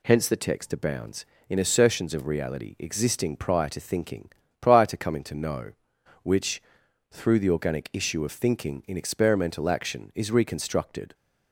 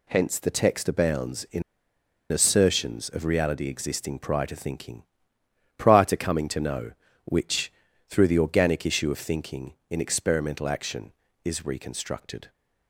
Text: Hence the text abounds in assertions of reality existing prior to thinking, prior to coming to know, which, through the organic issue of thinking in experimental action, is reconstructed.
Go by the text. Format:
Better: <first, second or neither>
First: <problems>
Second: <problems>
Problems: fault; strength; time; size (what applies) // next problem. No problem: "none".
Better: first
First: none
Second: pauses between "in" and "assertions"; noticeable; at 1.6 s; 0.68 s long